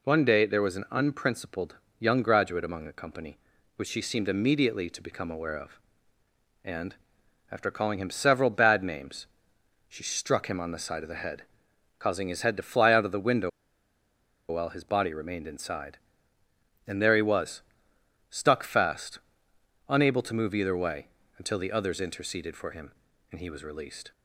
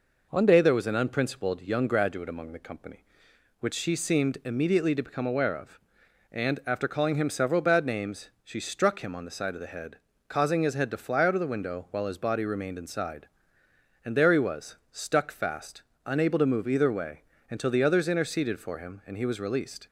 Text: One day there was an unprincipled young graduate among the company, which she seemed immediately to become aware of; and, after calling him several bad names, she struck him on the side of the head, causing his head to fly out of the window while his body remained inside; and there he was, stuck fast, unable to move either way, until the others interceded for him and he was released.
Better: second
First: pauses between "unprincipled" and "young"; slight; at 1.7 s; 0.24 s long // pauses between "window" and "while"; at 13.4 s; 1.0 s long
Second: none

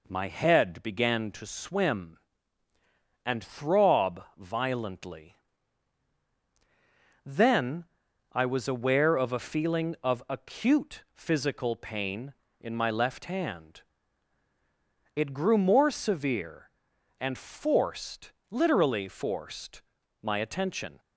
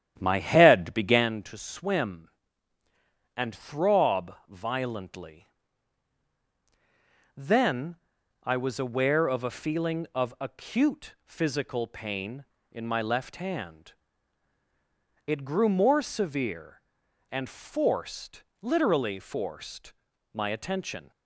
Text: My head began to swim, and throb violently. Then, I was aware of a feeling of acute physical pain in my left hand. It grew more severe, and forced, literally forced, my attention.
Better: first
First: pauses between "throb" and "violently"; slight; at 4.2 s; 0.16 s long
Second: starts louder than the rest; strong; until 1.3 s; 10 dB // pauses between "throb" and "violently"; slight; at 4.3 s; 0.16 s long

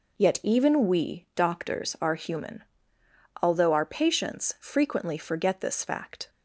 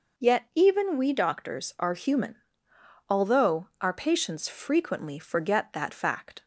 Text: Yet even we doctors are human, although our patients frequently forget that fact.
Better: second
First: says "this" for "that"; at 5.6 s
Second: none

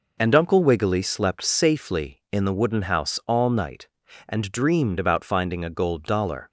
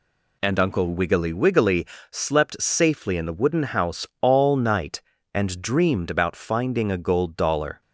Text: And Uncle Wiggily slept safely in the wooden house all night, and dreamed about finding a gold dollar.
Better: first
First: none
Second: says "Wiggily" twice; at 1.3 s

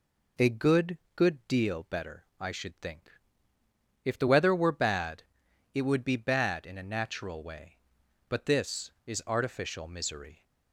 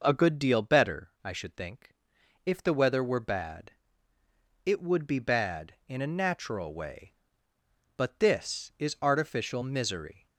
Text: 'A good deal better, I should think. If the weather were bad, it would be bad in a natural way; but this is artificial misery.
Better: second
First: says "good" twice; at 1.1 s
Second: none

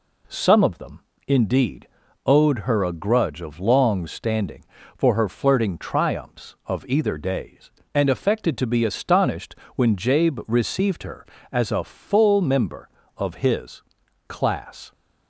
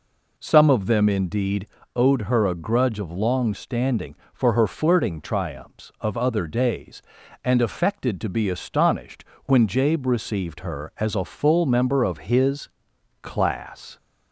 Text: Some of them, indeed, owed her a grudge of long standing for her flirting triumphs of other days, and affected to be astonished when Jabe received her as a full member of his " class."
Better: second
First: says "either" for "other"; at 6.8 s // pauses between "astonished" and "when"; slight; at 9.5 s; 0.22 s long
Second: pauses between "astonished" and "when"; slight; at 9.2 s; 0.20 s long

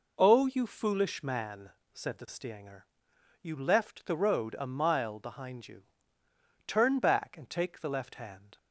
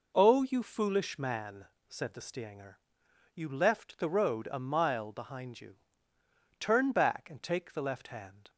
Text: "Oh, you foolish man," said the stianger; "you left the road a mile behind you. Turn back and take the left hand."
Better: neither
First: none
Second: none

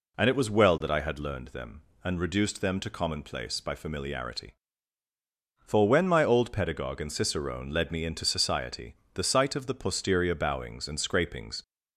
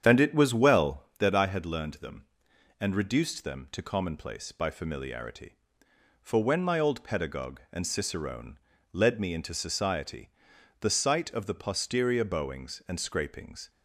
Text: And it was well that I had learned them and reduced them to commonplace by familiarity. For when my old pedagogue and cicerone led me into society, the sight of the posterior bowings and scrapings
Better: first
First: none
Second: starts louder than the rest; strong; until 1.3 s; 8.5 dB // pauses between "cicerone" and "led"; slight; at 8.5 s; 0.33 s long

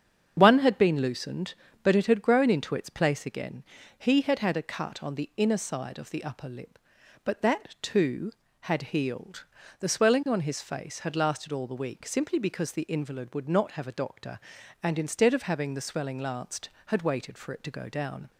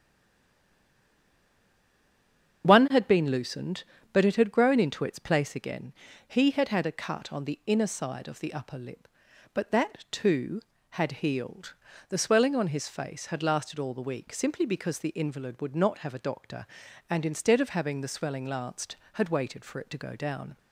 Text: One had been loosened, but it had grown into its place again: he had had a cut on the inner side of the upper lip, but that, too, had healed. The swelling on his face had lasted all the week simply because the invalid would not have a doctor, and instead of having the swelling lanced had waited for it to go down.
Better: first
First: starts louder than the rest; strong; until 1.3 s; 7.5 dB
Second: stays silent before the first word; strong; until 2.6 s; 2.6 s long // starts louder than the rest; strong; until 3.6 s; 7.5 dB

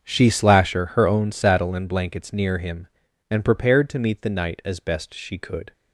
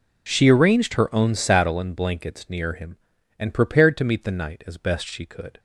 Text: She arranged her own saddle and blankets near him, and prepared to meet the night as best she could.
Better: second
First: starts louder than the rest; strong; until 1.1 s; 7.5 dB // says "slasher" for "arranged"; at 0.3 s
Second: none

